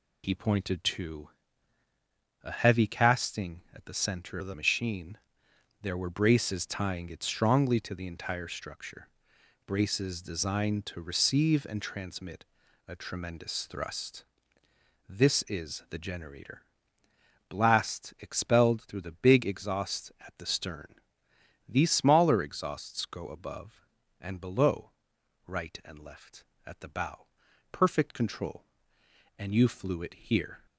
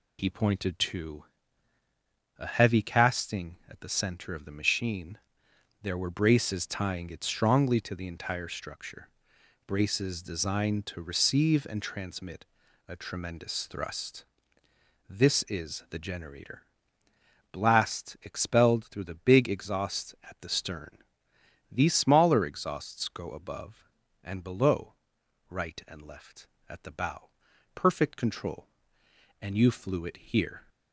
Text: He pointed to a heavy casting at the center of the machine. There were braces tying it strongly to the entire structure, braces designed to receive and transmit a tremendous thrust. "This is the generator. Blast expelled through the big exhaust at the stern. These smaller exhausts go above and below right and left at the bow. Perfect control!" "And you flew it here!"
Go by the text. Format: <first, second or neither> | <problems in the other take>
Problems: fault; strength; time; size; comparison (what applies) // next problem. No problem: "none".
second | pauses between "to" and "a"; at 1.2 s; 1.1 s long; also in the second // changes voice from "of" to "the"; from 4.3 to 4.5 s; 0.2 s long // pauses between "transmit" and "a"; at 12.4 s; 0.42 s long; also in the second // pauses between "below" and "right"; noticeable; at 24.9 s; 0.54 s long; noticeable in the second